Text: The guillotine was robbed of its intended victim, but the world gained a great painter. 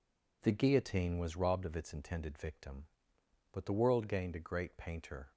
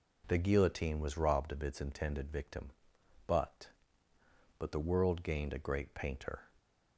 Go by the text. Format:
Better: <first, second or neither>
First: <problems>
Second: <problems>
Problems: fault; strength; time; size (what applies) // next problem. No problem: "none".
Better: first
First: none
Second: says "but" twice; at 4.5 s